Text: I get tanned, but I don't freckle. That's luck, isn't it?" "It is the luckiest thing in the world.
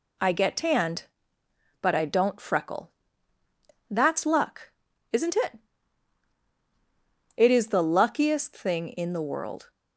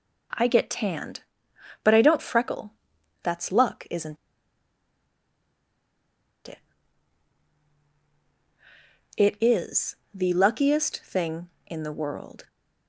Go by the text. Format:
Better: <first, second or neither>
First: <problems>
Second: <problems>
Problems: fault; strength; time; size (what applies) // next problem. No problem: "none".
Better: first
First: none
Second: pauses between "isn't" and "it"; strong; at 4.1 s; 2.3 s long // pauses between "is" and "the"; slight; at 9.9 s; 0.18 s long